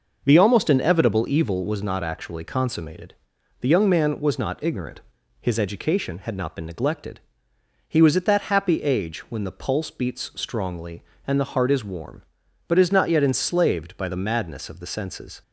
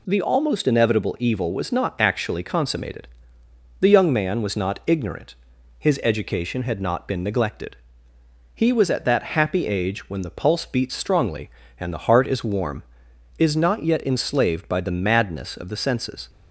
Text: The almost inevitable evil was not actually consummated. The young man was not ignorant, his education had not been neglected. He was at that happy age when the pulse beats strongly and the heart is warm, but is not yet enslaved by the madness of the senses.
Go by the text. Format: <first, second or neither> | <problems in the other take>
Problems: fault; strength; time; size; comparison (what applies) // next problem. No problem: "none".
first | skips "but"; at 13.1 s